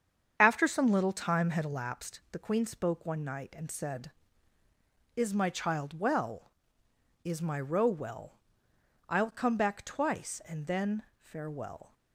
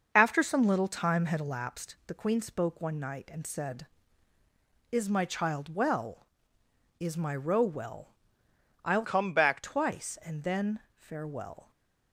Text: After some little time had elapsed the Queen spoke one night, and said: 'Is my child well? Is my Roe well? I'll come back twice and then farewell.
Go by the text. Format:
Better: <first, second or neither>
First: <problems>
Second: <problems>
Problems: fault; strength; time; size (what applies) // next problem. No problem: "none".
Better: first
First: starts louder than the rest; strong; until 1.4 s; 7.5 dB // pauses between "then" and "farewell"; slight; at 11.0 s; 0.16 s long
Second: starts louder than the rest; noticeable; until 1.1 s; 6 dB // changes voice from "come" to "back"; from 9.0 to 9.6 s; 0.6 s long // pauses between "then" and "farewell"; slight; at 10.8 s; 0.16 s long